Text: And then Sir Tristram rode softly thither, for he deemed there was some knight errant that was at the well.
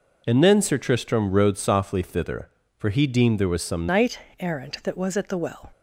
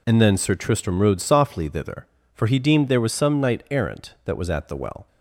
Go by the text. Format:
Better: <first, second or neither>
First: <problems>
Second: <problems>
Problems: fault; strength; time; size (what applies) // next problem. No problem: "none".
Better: second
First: changes voice at "knight"; from 3.8 s on; 1.9 s long // pauses between "knight" and "errant"; slight; at 4.1 s; 0.20 s long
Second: none